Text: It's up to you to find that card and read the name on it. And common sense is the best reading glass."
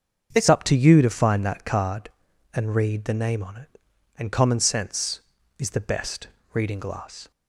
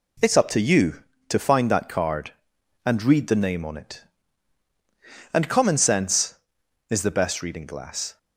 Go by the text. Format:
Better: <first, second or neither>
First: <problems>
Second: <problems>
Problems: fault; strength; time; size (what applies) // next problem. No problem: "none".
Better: second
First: starts louder than the rest; until 1.3 s; 6.5 dB // changes voice at "up"; from 0.4 s on; 6.9 s long // pauses between "best" and "reading"; slight; at 6.2 s; 0.24 s long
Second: none